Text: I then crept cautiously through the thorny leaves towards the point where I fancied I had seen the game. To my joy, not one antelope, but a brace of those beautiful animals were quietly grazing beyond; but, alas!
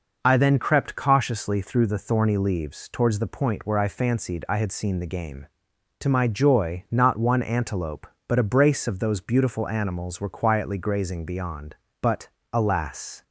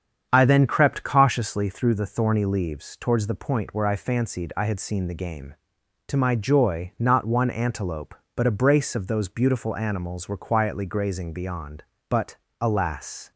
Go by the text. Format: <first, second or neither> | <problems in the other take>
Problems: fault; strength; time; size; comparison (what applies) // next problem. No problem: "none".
first | starts louder than the rest; strong; until 1.6 s; 8 dB